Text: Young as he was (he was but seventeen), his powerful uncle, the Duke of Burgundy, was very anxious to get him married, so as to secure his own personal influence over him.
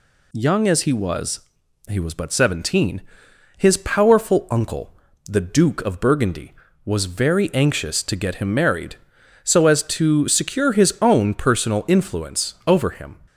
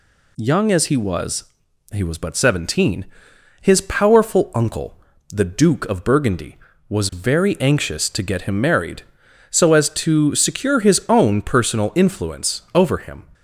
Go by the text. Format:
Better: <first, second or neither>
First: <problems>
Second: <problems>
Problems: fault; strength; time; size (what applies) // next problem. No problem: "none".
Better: neither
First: none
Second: none